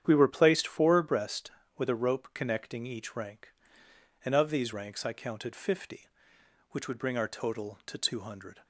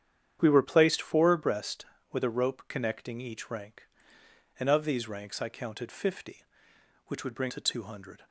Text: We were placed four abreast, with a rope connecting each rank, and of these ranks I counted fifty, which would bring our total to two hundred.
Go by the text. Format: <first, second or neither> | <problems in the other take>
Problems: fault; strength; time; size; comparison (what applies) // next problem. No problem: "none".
first | starts louder than the rest; strong; until 1.4 s; 9 dB; strong in the first // skips "our total"; at 7.4 s